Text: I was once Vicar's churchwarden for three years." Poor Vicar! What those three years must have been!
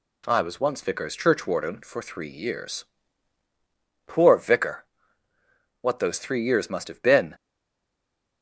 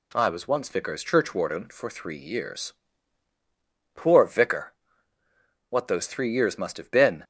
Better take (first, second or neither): second